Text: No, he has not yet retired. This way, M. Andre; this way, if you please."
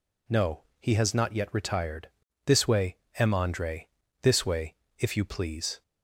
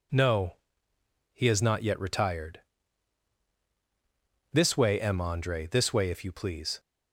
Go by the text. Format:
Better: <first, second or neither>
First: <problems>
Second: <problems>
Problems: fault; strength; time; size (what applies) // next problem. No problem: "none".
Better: neither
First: none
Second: none